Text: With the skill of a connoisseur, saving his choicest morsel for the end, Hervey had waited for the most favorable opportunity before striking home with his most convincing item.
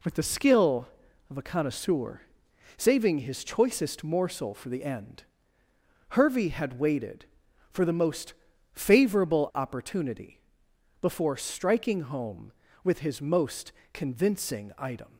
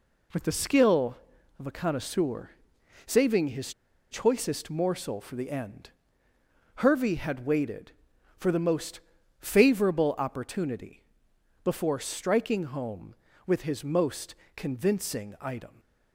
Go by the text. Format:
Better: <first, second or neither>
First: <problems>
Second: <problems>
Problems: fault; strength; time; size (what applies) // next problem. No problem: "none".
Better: first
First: pauses between "most" and "favorable"; at 8.3 s; 0.40 s long // pauses between "opportunity" and "before"; noticeable; at 10.4 s; 0.60 s long // pauses between "most" and "convincing"; slight; at 13.7 s; 0.22 s long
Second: pauses between "his" and "choicest"; at 3.7 s; 0.38 s long // pauses between "most" and "favorable"; at 8.9 s; 0.40 s long // pauses between "opportunity" and "before"; noticeable; at 11.0 s; 0.60 s long // pauses between "most" and "convincing"; slight; at 14.3 s; 0.22 s long